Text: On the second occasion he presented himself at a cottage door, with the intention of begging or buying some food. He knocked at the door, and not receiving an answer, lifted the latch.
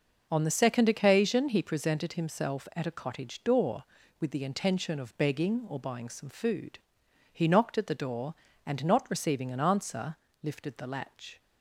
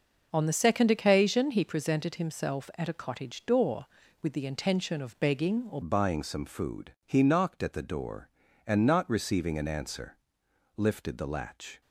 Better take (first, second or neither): first